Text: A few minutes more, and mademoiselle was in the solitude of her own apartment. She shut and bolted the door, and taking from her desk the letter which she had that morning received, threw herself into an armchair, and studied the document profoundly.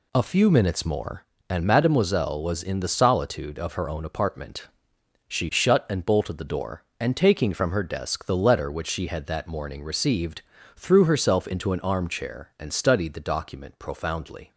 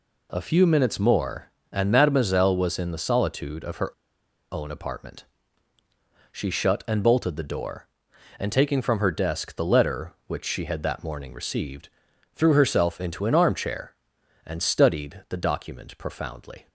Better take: first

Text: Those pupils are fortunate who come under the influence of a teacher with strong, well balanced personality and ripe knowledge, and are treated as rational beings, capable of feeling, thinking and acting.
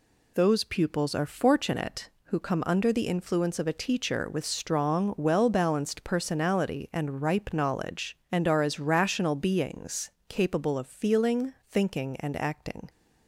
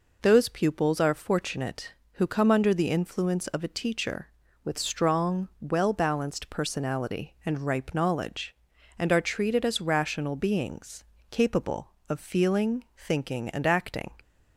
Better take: second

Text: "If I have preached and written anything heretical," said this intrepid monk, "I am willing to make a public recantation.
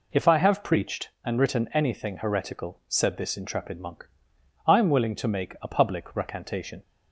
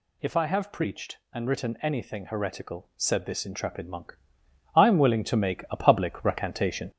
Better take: first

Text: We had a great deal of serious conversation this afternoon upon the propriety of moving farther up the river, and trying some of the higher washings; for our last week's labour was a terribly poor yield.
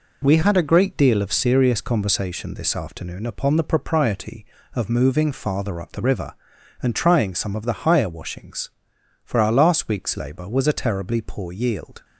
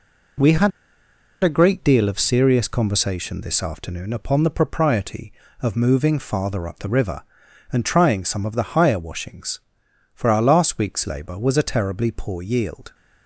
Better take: first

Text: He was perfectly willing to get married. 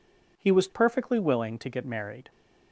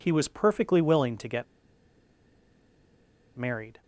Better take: first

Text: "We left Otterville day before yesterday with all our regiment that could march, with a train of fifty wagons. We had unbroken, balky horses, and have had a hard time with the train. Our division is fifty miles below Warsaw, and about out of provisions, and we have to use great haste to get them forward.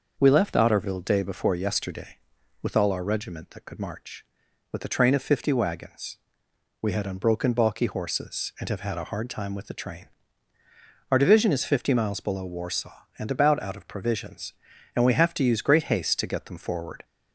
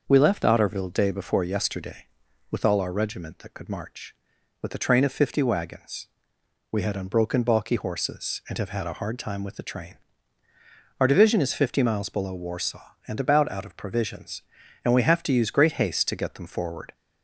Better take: neither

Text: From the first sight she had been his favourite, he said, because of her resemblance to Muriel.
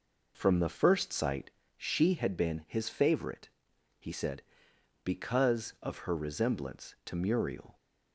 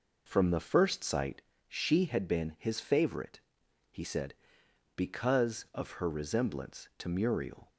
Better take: neither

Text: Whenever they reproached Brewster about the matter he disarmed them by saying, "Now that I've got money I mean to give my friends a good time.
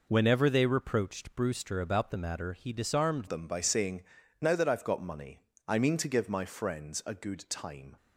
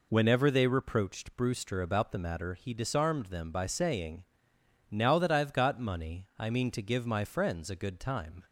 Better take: second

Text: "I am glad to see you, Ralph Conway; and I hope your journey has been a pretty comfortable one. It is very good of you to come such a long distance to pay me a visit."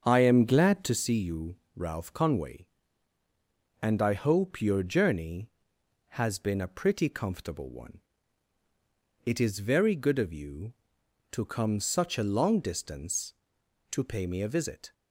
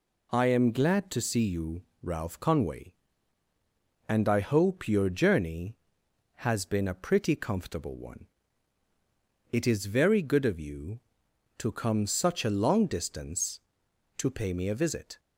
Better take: second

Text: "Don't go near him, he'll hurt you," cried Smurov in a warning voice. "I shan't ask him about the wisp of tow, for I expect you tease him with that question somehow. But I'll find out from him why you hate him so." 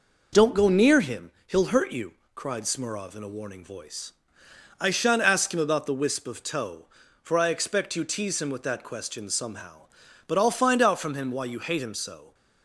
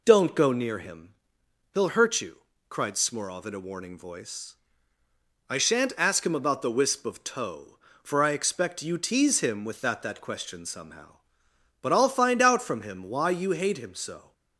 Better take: first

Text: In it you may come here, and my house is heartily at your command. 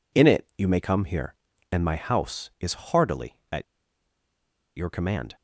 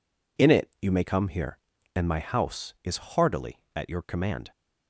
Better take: second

